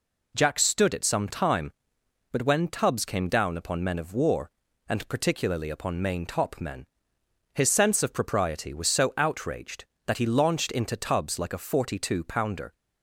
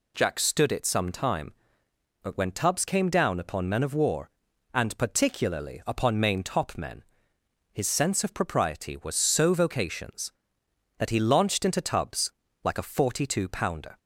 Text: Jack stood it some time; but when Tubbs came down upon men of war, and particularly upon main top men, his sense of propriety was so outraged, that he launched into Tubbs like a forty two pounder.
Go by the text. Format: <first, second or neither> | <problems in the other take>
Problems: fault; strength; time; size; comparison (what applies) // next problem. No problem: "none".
first | says "vocations" for "outraged"; at 9.5 s // pauses between "Tubbs" and "like"; slight; at 12.3 s; 0.32 s long